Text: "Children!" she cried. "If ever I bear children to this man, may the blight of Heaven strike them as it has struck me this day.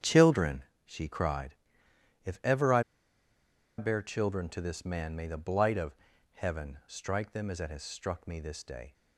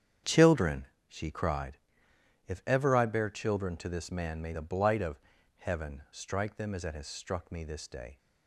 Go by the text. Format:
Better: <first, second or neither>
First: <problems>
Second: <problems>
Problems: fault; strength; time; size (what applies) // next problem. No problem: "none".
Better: second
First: starts louder than the rest; strong; until 1.2 s; 8.5 dB // pauses between "I" and "bear"; noticeable; at 2.8 s; 0.96 s long // pauses between "of" and "Heaven"; at 5.9 s; 0.38 s long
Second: starts louder than the rest; strong; until 1.4 s; 8.5 dB // pauses between "of" and "Heaven"; at 5.1 s; 0.38 s long